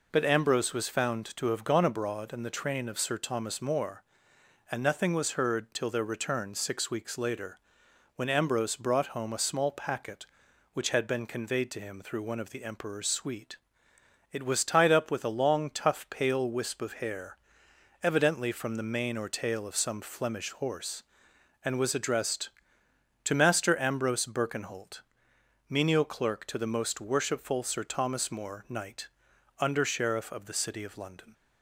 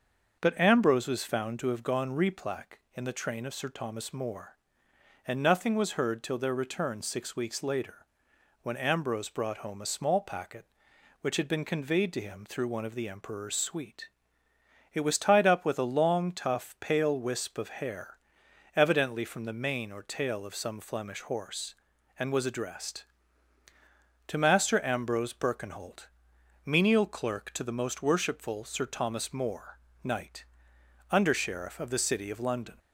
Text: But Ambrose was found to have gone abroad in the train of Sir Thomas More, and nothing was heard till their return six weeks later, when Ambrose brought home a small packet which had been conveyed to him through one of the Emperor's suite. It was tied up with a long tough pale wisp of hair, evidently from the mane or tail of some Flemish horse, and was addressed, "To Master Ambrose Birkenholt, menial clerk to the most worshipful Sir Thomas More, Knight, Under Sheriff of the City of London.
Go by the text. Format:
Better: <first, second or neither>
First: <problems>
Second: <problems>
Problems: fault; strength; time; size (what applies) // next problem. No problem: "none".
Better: first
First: none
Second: starts louder than the rest; until 1.4 s; 6.5 dB // says "replac" for "abroad"; at 2.1 s